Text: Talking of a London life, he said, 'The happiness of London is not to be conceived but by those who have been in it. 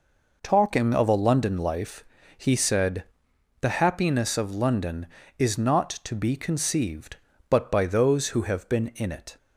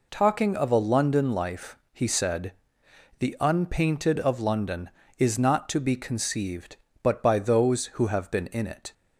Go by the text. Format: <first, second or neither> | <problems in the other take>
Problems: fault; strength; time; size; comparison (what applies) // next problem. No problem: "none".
first | says "unpainted" for "happiness"; at 3.3 s